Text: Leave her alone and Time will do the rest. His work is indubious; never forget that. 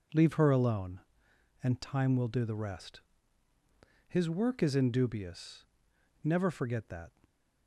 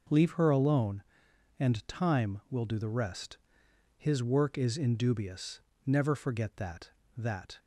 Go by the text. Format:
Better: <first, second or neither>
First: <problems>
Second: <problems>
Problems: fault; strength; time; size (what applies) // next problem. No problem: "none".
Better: first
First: none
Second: starts louder than the rest; until 1.6 s; 6.5 dB // says "that" twice; at 7.1 s